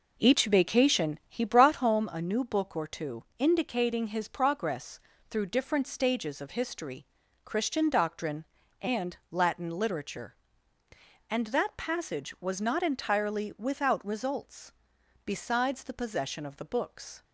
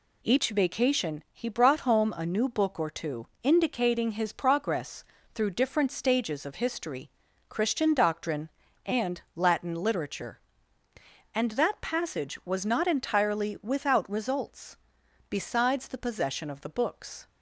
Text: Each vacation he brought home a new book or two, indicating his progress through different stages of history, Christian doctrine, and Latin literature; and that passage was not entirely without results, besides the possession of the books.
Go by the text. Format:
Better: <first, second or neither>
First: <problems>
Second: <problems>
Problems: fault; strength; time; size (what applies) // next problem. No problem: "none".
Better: second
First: starts louder than the rest; noticeable; until 1.9 s; 4.5 dB // pauses between "progress" and "through"; slight; at 4.9 s; 0.30 s long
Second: pauses between "progress" and "through"; slight; at 5.0 s; 0.30 s long